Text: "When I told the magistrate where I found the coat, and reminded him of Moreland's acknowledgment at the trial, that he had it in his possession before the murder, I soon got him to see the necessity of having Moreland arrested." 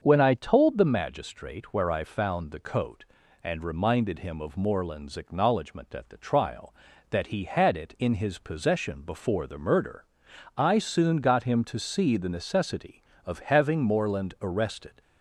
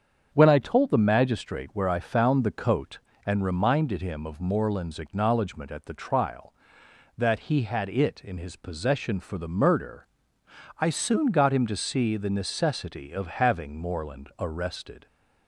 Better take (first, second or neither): first